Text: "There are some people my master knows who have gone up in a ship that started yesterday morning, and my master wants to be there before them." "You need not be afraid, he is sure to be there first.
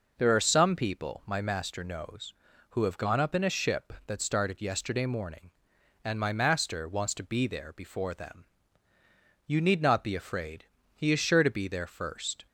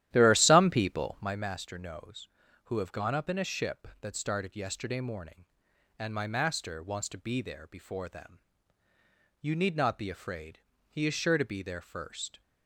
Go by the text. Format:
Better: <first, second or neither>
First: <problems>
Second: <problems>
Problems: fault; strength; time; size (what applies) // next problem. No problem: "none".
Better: first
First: none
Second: starts louder than the rest; strong; until 1.4 s; 12.5 dB